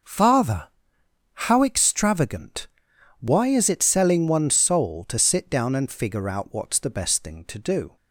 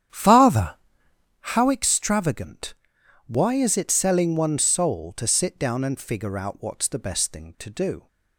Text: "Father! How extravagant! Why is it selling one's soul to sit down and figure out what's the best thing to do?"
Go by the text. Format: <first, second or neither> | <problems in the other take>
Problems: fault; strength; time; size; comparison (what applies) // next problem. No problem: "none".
first | starts louder than the rest; strong; until 1.5 s; 9.5 dB